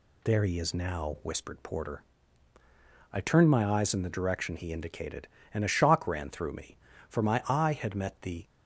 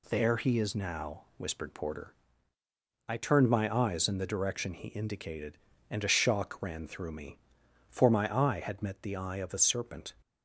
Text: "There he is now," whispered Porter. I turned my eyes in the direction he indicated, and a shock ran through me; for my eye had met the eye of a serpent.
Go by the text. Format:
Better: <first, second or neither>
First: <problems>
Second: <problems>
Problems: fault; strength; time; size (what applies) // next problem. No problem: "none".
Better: second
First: stops before "eye of a serpent"; at 8.4 s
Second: none